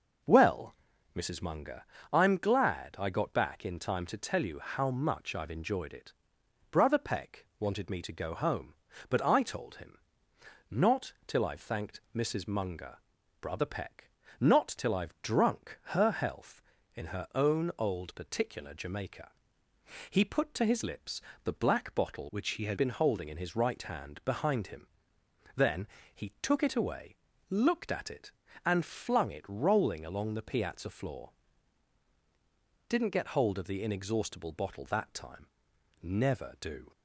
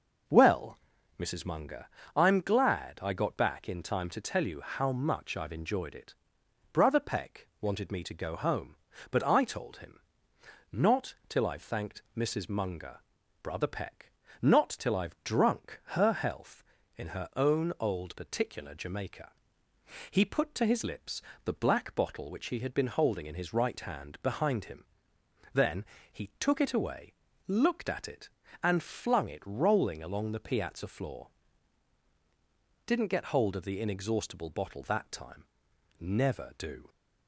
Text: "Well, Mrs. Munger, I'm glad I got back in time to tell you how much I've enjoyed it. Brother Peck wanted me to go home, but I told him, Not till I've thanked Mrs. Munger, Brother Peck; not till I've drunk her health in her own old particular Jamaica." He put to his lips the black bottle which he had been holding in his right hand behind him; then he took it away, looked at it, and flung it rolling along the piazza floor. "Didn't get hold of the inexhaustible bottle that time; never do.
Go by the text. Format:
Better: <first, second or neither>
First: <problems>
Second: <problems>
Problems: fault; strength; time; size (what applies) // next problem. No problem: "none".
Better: second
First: pauses between "lips" and "the"; slight; at 21.2 s; 0.24 s long // changes voice from "which" to "had"; from 22.2 to 22.7 s; 0.5 s long // pauses between "then" and "he"; slight; at 25.8 s; 0.26 s long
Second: pauses between "lips" and "the"; slight; at 21.2 s; 0.24 s long // pauses between "then" and "he"; slight; at 25.8 s; 0.26 s long